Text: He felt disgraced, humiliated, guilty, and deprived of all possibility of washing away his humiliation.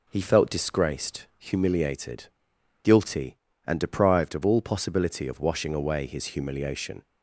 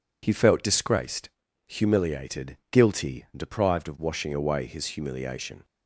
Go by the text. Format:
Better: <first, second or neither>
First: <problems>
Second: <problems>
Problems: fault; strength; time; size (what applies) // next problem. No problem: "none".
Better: first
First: none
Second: skips "all possibility of"; at 3.9 s